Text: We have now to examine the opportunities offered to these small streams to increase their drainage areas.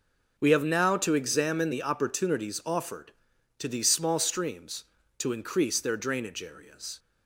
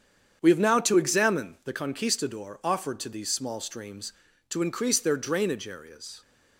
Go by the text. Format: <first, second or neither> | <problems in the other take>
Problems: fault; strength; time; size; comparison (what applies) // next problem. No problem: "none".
first | starts louder than the rest; strong; until 1.4 s; 8 dB // says "conquistador" for "opportunities"; at 1.7 s